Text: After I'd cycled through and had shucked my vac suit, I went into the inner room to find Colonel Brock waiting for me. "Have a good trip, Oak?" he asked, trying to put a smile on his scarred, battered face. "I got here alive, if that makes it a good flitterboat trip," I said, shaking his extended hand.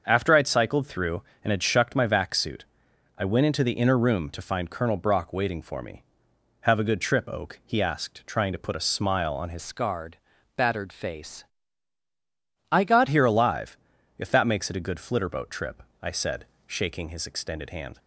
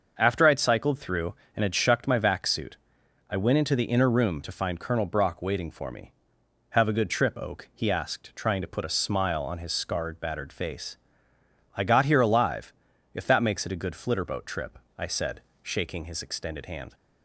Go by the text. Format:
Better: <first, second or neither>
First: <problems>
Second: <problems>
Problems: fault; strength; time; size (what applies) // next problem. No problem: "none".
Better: second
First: starts louder than the rest; until 1.0 s; 6.5 dB // changes voice from "scarred" to "got"; from 9.5 to 13.0 s; 3.5 s long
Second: starts louder than the rest; until 1.1 s; 6.5 dB